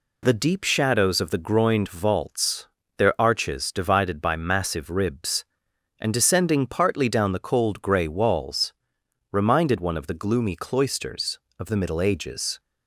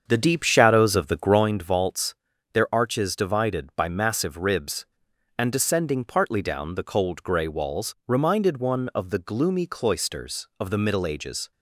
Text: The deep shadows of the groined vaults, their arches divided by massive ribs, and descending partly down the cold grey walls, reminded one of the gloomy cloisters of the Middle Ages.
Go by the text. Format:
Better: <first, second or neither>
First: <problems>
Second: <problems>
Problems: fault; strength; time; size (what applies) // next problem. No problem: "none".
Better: first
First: none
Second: starts louder than the rest; strong; until 1.6 s; 7 dB